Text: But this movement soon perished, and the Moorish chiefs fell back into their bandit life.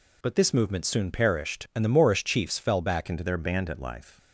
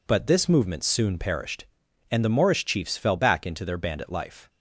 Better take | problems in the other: second | changes voice at "into"; from 3.0 s on; 1.1 s long

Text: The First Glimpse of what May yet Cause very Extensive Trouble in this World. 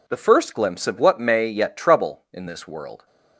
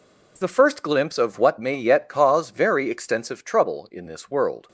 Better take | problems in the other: second | skips "Cause very Extensive"; at 1.7 s

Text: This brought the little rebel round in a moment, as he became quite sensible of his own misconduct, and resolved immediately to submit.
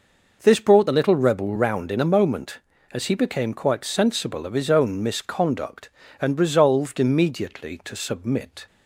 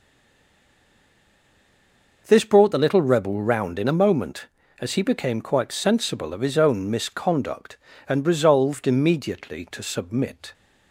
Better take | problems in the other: first | stays silent before the first word; until 2.2 s; 2.2 s long

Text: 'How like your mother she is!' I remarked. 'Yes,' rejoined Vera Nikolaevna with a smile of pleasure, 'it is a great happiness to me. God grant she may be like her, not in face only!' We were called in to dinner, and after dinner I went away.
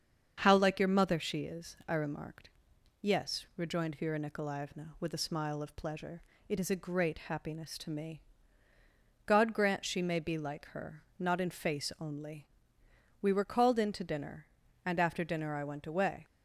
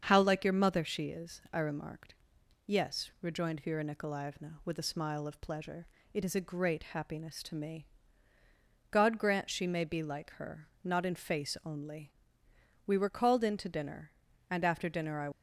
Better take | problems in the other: first | starts louder than the rest; until 1.0 s; 7 dB; also in the first // stops before "went away"; at 15.3 s

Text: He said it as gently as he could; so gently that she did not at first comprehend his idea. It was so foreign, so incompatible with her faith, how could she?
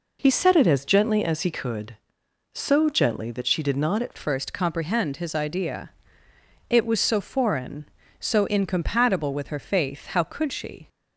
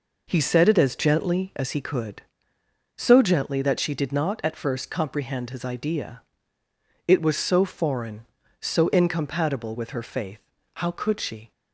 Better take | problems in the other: second | changes voice at "first"; from 4.1 s on; 6.7 s long

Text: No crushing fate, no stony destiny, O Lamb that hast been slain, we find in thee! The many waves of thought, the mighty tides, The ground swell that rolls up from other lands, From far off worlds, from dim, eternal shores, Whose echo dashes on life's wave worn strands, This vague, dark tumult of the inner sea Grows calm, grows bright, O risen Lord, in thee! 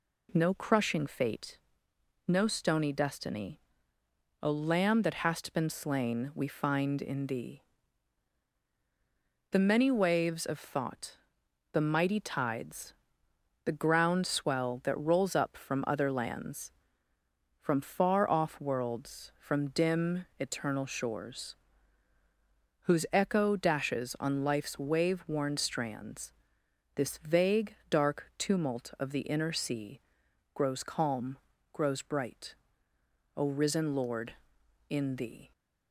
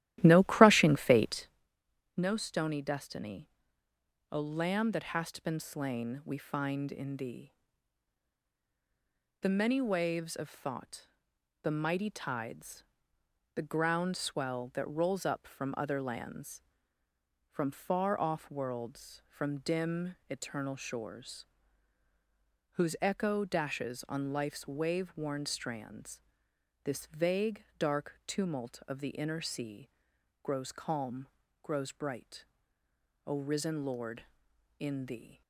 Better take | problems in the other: first | starts louder than the rest; strong; until 1.7 s; 14 dB // pauses between "sea" and "Grows"; noticeable; at 29.8 s; 0.52 s long; noticeable in the first

